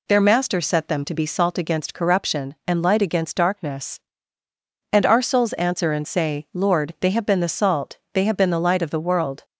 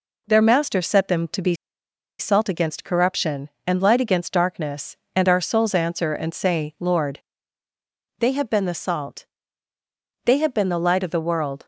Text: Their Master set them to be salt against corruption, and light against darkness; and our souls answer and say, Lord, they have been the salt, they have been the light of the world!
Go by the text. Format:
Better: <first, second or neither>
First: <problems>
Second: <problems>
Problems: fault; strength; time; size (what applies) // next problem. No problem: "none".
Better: first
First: none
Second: pauses between "be" and "salt"; noticeable; at 1.5 s; 0.65 s long